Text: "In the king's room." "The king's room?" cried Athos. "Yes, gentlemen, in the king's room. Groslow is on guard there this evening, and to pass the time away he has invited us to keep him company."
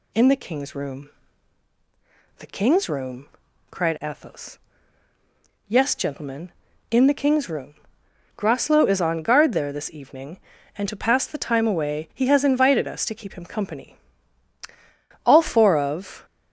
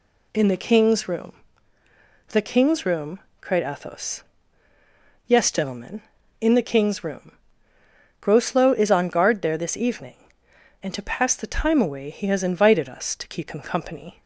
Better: second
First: goes on to say "All four of"; noticeable; from 15.2 s on; 1.0 s long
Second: none

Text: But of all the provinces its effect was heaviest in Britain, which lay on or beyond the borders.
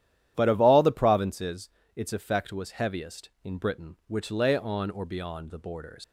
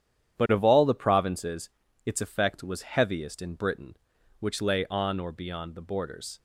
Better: second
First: starts louder than the rest; strong; until 1.3 s; 11.5 dB // pauses between "provinces" and "its"; slight; at 1.6 s; 0.26 s long // leaves "borders" unfinished; at 6.0 s; 115 ms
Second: starts louder than the rest; strong; until 1.4 s; 9.5 dB // pauses between "provinces" and "its"; slight; at 1.6 s; 0.36 s long

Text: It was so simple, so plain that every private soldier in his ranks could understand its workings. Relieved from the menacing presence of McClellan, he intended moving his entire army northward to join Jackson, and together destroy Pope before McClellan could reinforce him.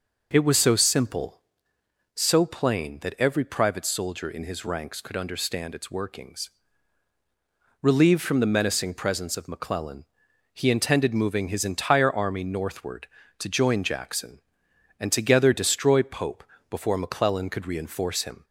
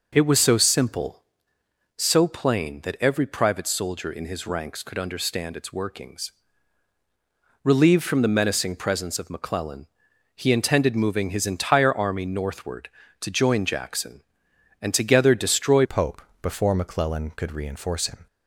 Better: first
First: pauses between "Pope" and "before"; slight; at 16.4 s; 0.26 s long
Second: changes voice at "Pope"; from 15.8 s on; 2.4 s long // pauses between "Pope" and "before"; slight; at 16.2 s; 0.20 s long

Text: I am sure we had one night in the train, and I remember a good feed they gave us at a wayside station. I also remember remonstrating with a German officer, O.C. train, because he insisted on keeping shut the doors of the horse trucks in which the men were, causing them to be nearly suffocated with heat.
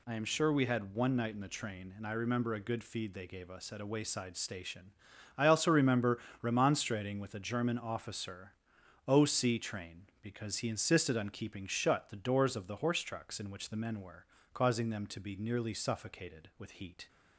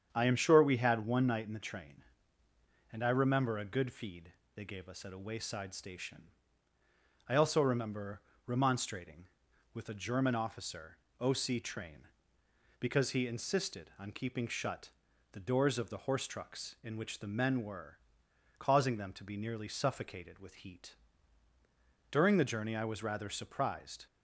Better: first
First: pauses between "remember" and "remonstrating"; slight; at 6.1 s; 0.24 s long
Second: starts louder than the rest; strong; until 1.1 s; 8 dB // pauses between "feed" and "they"; slight; at 4.3 s; 0.24 s long // pauses between "remember" and "remonstrating"; slight; at 8.2 s; 0.24 s long // pauses between "shut" and "the"; at 14.9 s; 0.40 s long // goes on to say "During the journey I was rather surprised"; strong; from 22.1 s on; 1.9 s long

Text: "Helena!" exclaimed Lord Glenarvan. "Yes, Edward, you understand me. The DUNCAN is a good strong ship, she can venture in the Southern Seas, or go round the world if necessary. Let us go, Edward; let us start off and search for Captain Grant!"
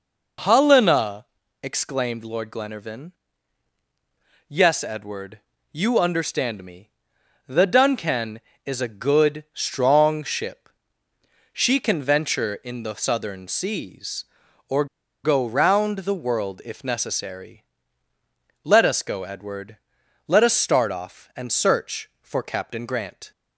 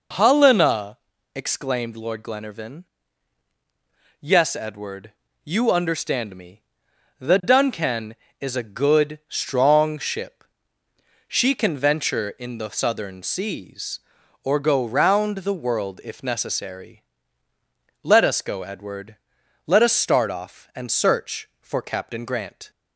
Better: second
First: pauses between "or" and "go"; at 14.8 s; 0.38 s long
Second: none

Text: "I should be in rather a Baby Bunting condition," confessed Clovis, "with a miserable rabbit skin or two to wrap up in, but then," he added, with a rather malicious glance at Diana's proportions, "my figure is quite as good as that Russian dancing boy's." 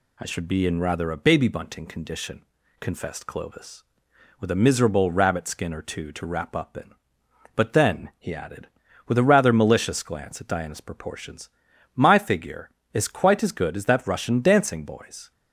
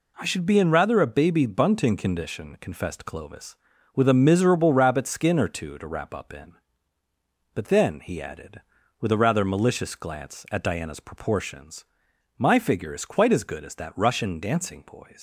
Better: first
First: none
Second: leaves "boy's" unfinished; at 15.1 s; 115 ms

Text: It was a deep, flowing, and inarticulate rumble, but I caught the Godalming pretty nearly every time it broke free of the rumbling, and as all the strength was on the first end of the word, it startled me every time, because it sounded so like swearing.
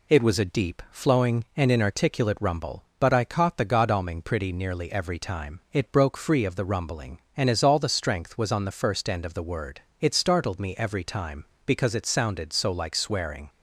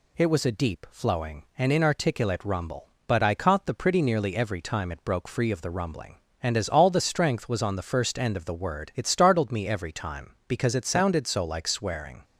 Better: first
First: none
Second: skips "Godalming"; at 3.7 s

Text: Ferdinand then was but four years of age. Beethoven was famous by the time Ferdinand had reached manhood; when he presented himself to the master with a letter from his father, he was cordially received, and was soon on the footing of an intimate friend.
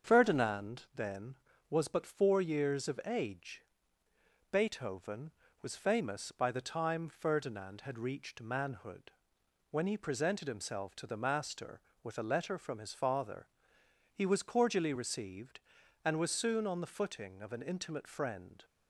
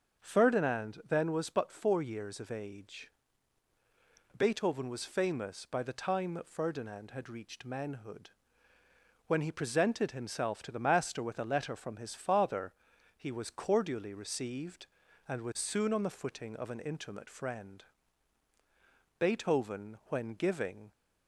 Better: first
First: starts louder than the rest; until 1.1 s; 7 dB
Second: starts louder than the rest; until 1.2 s; 6.5 dB // goes on to say "Beethoven when giving"; strong; from 19.1 s on; 1.7 s long

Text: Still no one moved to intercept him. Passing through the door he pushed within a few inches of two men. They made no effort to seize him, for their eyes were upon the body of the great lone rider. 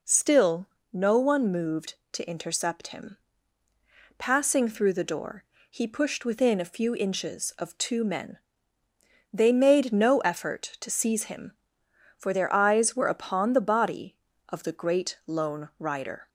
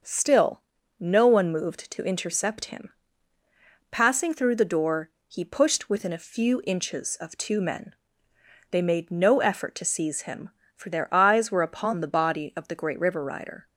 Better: first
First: pauses between "Still" and "no"; slight; at 0.6 s; 0.26 s long // pauses between "door" and "he"; slight; at 5.4 s; 0.26 s long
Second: starts louder than the rest; until 1.4 s; 6 dB // pauses between "Still" and "no"; at 0.5 s; 0.40 s long // pauses between "door" and "he"; slight; at 5.0 s; 0.18 s long // says "river" for "lone"; at 12.9 s

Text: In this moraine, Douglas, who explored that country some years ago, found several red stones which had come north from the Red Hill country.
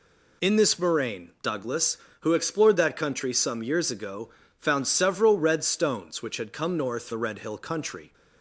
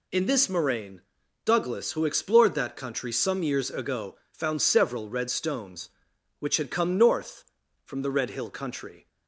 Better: second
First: skips "from"; at 7.1 s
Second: none

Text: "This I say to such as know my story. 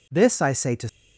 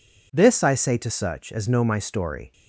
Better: second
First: stops before "such as know my story"; at 0.8 s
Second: none

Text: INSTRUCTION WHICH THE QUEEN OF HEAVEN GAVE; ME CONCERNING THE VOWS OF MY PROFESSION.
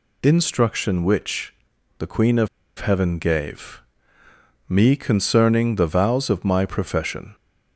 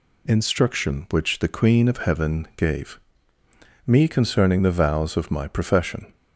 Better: second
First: pauses between "WHICH" and "THE"; at 1.5 s; 0.44 s long // pauses between "OF" and "HEAVEN"; slight; at 2.4 s; 0.30 s long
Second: none

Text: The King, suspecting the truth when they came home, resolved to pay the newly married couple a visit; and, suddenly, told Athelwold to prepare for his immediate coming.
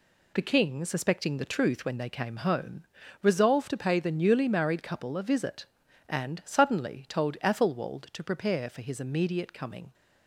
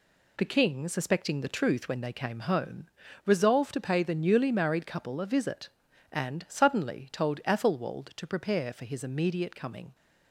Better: neither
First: none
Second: none

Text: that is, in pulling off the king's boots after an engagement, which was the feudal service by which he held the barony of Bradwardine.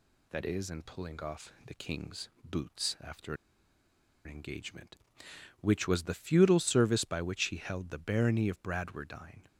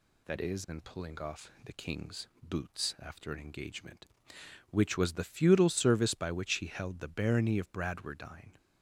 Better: second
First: pauses between "king's" and "boots"; slight; at 2.2 s; 0.16 s long // pauses between "after" and "an"; noticeable; at 3.3 s; 0.91 s long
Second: pauses between "king's" and "boots"; slight; at 2.2 s; 0.16 s long

